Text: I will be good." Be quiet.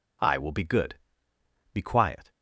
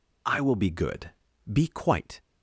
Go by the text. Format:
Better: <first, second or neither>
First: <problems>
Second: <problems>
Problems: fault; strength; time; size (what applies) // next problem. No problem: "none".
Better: first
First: none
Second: says "quite" for "quiet"; at 1.6 s